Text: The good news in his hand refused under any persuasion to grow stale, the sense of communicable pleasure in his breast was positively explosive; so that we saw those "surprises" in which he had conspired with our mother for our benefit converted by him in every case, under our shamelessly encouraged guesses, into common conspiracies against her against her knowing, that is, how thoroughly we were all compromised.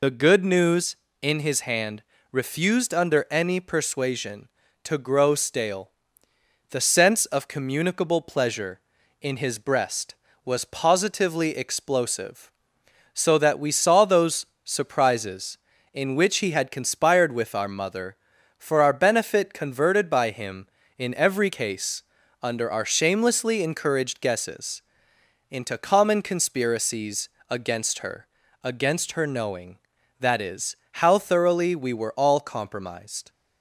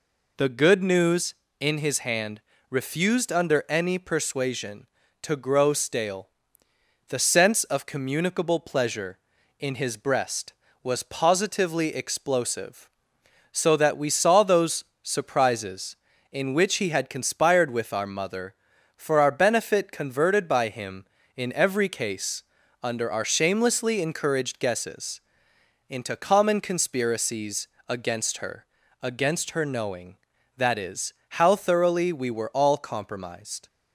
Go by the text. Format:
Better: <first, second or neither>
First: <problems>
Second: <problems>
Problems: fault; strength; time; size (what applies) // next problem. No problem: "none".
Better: second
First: loses the start of "The"; at 0.0 s; 30 ms // pauses between "hand" and "refused"; slight; at 2.0 s; 0.28 s long // pauses between "those" and "surprises"; slight; at 14.4 s; 0.18 s long // pauses between "conspiracies" and "against"; slight; at 27.2 s; 0.20 s long // pauses between "her" and "against"; slight; at 28.2 s; 0.34 s long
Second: pauses between "hand" and "refused"; slight; at 2.4 s; 0.28 s long // pauses between "those" and "surprises"; slight; at 14.8 s; 0.18 s long // pauses between "conspiracies" and "against"; slight; at 27.6 s; 0.20 s long // pauses between "her" and "against"; slight; at 28.6 s; 0.34 s long